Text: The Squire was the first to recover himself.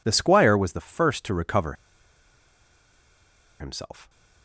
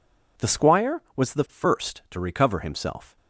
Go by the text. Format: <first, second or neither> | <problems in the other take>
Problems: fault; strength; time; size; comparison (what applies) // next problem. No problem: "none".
second | pauses between "recover" and "himself"; strong; at 1.7 s; 1.8 s long